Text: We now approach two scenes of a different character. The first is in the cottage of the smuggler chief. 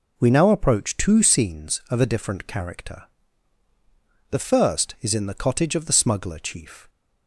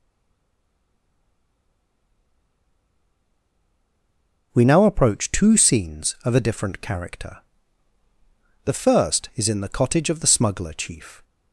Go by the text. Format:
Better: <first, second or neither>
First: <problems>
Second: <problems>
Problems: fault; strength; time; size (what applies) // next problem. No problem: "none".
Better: first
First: none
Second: stays silent before the first word; strong; until 4.5 s; 4.5 s long